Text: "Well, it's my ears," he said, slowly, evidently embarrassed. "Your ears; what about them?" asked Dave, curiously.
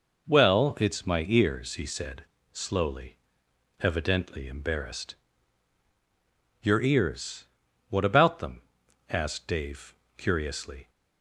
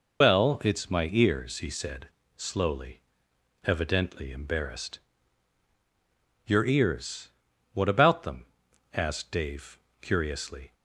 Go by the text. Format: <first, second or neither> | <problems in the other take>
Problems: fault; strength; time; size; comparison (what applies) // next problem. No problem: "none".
first | loses the start of "Well"; at 0.2 s; 95 ms